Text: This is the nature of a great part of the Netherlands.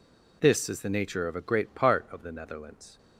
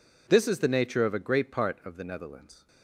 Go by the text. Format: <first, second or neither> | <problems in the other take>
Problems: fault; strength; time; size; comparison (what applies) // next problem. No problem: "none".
neither | none